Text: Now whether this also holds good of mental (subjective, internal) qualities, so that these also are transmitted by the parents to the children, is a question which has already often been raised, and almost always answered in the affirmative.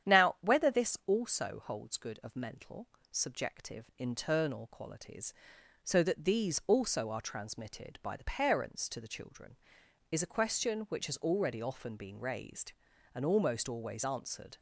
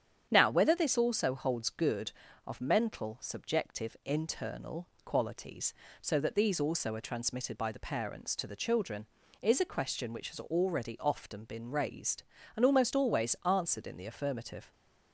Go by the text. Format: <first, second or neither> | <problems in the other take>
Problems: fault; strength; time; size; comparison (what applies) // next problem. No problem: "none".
second | starts louder than the rest; strong; until 1.2 s; 9.5 dB; strong in the second // stops before "in the affirmative"; at 14.5 s